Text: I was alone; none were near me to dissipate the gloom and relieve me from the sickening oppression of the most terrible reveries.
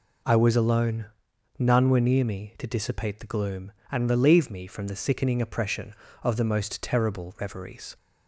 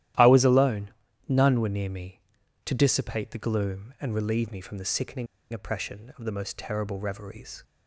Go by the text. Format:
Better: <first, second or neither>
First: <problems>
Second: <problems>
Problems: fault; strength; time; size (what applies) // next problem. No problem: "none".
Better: first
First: none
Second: starts louder than the rest; strong; until 1.5 s; 13 dB // pauses between "sickening" and "oppression"; slight; at 5.2 s; 0.25 s long